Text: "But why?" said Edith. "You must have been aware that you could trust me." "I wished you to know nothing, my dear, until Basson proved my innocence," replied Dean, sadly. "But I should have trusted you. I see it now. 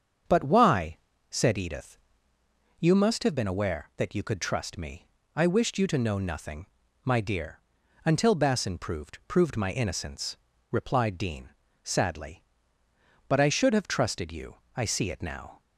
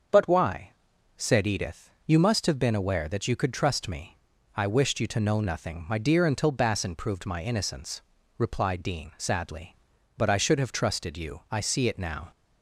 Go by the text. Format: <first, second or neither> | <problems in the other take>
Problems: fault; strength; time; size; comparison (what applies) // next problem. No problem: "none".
second | starts louder than the rest; until 1.6 s; 7 dB; also in the second // says "proved" twice; at 9.2 s